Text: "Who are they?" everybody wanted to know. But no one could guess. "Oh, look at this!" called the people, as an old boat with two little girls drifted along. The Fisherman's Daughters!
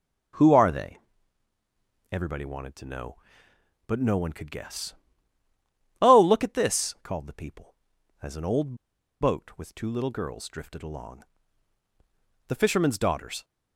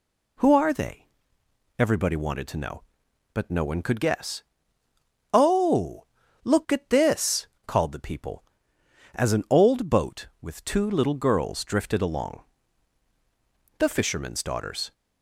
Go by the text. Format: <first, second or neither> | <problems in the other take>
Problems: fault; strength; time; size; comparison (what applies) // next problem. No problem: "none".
second | starts louder than the rest; strong; until 2.5 s; 7.5 dB // pauses between "old" and "boat"; noticeable; at 8.7 s; 0.46 s long